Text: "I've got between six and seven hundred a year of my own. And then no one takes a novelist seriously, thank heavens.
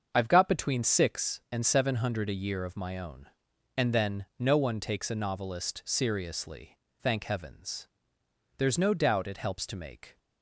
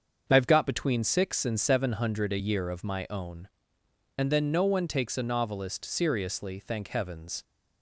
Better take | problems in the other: second | starts louder than the rest; until 1.1 s; 6.5 dB; also in the second // goes on to say "There's no doubt it helps to make"; from 8.5 s on; 1.6 s long

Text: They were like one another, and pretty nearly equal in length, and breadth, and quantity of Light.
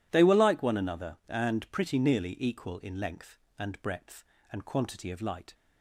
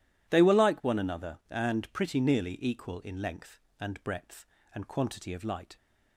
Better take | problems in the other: neither | none

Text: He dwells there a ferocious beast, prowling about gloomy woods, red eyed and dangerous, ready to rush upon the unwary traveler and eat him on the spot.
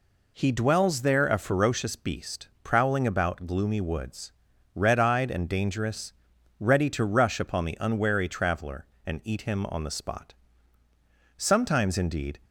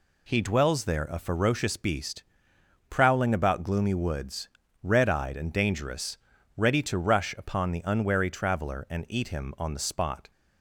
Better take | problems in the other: second | goes on to say "Sometimes indeed"; noticeable; from 11.3 s on; 1.0 s long

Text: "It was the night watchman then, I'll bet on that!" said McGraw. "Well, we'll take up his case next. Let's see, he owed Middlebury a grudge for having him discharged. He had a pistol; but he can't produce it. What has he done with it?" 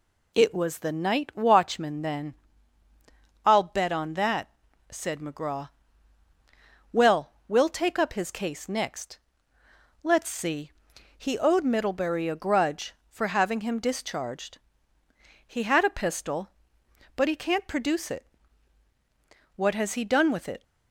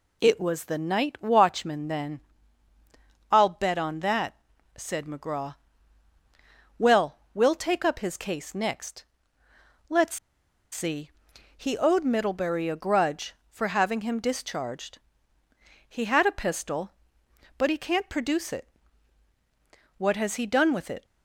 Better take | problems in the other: first | pauses between "Let's" and "see"; noticeable; at 10.1 s; 0.54 s long

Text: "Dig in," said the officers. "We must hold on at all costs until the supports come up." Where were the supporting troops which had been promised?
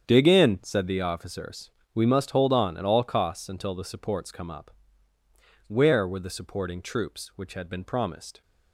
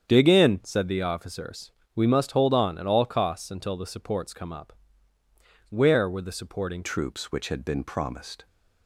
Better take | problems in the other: first | starts louder than the rest; strong; until 1.0 s; 8 dB; strong in the first // changes voice at "troops"; from 6.8 s on; 1.6 s long

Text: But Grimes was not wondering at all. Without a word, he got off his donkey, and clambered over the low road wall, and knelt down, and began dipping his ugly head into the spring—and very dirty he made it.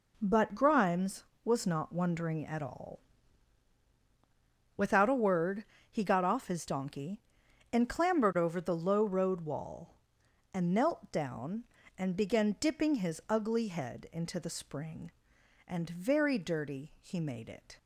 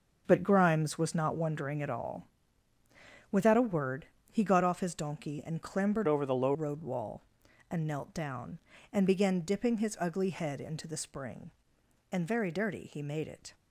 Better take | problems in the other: first | starts louder than the rest; noticeable; until 1.2 s; 6 dB // changes voice from "over" to "low"; from 6.0 to 6.5 s; 0.5 s long

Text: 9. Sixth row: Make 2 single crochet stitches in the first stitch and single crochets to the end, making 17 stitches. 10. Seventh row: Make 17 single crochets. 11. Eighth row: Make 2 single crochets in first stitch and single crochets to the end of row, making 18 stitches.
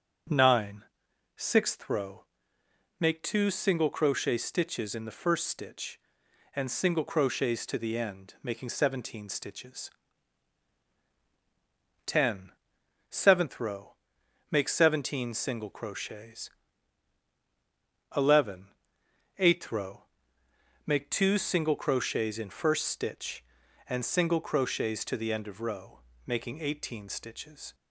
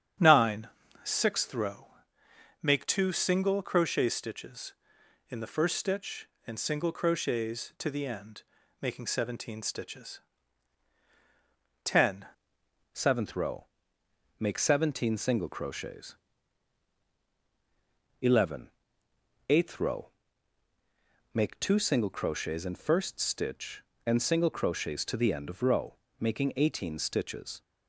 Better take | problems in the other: first | starts louder than the rest; strong; until 1.5 s; 8.5 dB; also in the first // changes voice at "Seventh"; from 12.9 s on; 14.7 s long

